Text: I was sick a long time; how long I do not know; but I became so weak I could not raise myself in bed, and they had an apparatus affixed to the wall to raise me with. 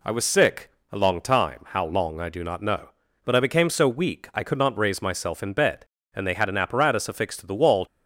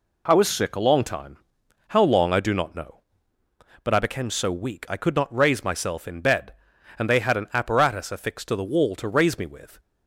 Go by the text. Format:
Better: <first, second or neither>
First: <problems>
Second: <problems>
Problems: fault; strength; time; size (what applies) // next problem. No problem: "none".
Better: second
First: pauses between "sick" and "a"; slight; at 0.7 s; 0.20 s long // stops before "to raise me with"; at 7.8 s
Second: none